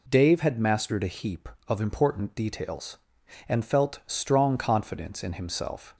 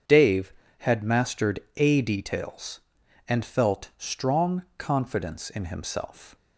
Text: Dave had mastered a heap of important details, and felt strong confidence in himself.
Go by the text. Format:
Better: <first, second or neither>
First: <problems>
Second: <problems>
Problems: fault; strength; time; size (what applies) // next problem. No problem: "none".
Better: first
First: none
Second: starts louder than the rest; strong; until 1.3 s; 7.5 dB // pauses between "mastered" and "a"; slight; at 1.5 s; 0.18 s long // skips "heap of important"; at 2.0 s